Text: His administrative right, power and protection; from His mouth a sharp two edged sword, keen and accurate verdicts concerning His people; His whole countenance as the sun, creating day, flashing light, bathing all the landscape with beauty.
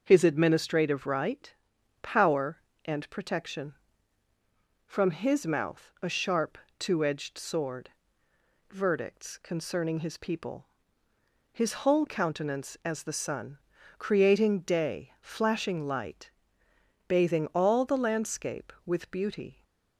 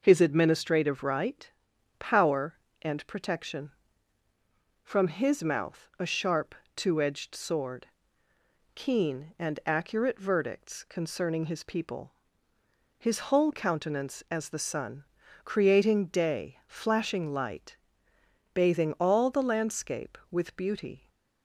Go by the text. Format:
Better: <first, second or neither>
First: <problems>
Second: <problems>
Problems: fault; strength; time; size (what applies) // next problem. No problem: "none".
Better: second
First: starts louder than the rest; until 1.0 s; 6.5 dB // pauses between "sharp" and "two"; slight; at 6.5 s; 0.20 s long // skips "keen and accurate"; at 8.2 s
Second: pauses between "sharp" and "two"; slight; at 6.5 s; 0.20 s long